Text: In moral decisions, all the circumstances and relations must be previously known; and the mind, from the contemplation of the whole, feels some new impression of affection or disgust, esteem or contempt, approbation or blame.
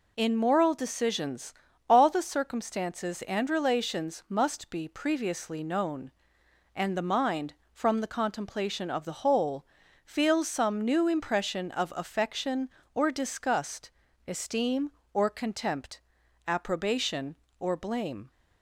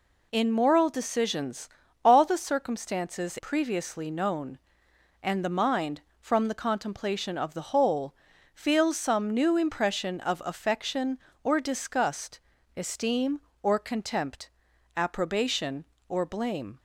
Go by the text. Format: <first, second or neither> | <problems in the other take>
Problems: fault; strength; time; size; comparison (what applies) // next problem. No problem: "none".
first | skips "and relations must be"; at 3.3 s